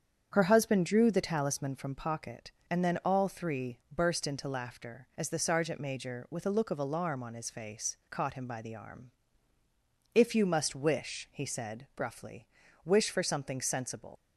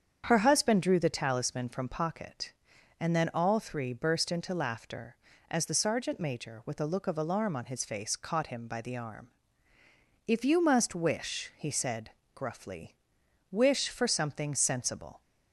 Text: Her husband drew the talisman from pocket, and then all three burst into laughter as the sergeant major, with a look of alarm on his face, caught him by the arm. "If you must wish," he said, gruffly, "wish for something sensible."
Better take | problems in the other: second | starts louder than the rest; strong; until 1.3 s; 8 dB; strong in the second // pauses between "three" and "burst"; slight; at 3.7 s; 0.18 s long // leaves "sensible" unfinished; at 14.1 s; 110 ms

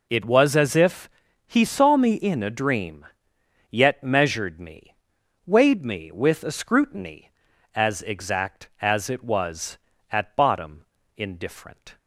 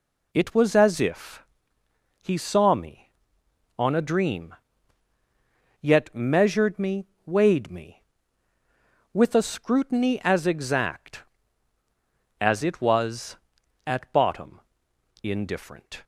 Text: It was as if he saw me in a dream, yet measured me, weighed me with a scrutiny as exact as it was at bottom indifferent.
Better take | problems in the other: first | pauses between "if" and "he"; noticeable; at 1.4 s; 0.80 s long; also in the first // says "on" for "in"; at 3.7 s // pauses between "bottom" and "indifferent"; noticeable; at 14.6 s; 0.60 s long; slight in the first

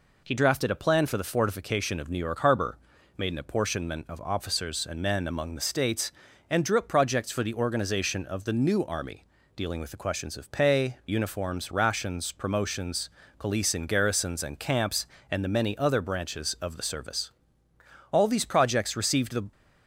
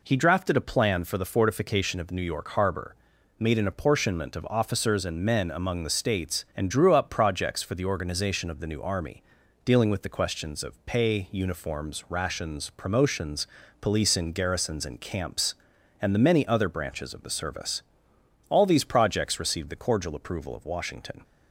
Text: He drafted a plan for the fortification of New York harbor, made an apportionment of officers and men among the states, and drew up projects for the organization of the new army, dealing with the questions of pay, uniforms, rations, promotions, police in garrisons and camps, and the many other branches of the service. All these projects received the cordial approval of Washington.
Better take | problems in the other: second | stops before "cordial approval of Washington"; at 19.5 s

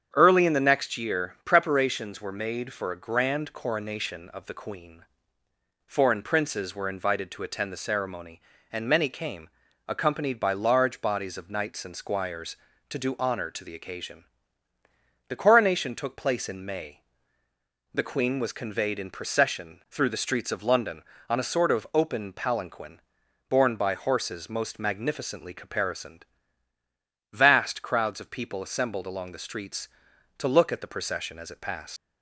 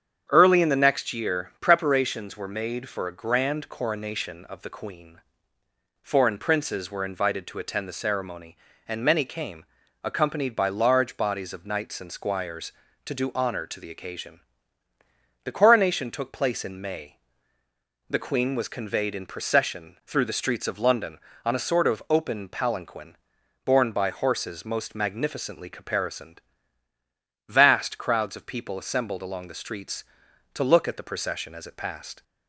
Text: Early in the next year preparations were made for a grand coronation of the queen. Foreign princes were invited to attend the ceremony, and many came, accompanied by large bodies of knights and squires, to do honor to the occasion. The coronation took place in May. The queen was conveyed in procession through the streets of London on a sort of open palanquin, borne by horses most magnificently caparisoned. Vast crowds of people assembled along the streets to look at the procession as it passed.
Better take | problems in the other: second | starts louder than the rest; strong; until 1.1 s; 8 dB; strong in the second // leaves "passed" unfinished; at 31.9 s; 105 ms

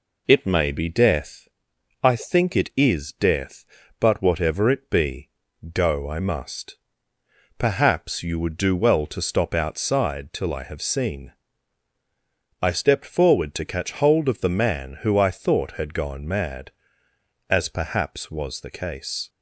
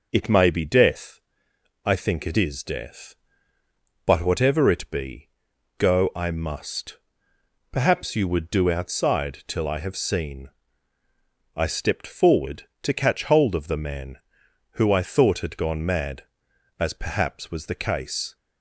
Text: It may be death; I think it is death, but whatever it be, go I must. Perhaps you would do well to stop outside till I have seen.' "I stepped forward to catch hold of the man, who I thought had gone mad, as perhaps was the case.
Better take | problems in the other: first | skips "well to stop"; at 8.7 s

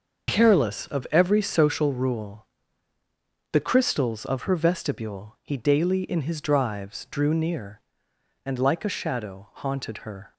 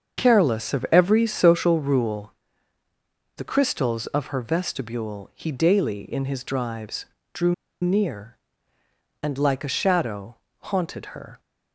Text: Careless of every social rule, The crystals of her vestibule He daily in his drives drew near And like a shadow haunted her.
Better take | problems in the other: first | starts louder than the rest; until 1.2 s; 7 dB // pauses between "drives" and "drew"; slight; at 7.0 s; 0.28 s long // pauses between "drew" and "near"; slight; at 7.5 s; 0.27 s long // pauses between "shadow" and "haunted"; slight; at 10.3 s; 0.24 s long

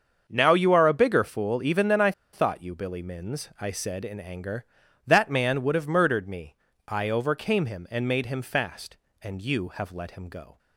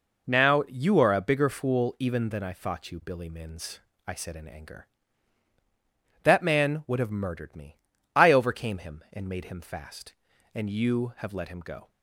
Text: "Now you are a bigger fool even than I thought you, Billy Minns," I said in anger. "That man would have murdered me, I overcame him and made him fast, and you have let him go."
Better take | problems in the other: second | starts louder than the rest; until 1.2 s; 7 dB // pauses between "I" and "thought"; slight; at 2.1 s; 0.22 s long

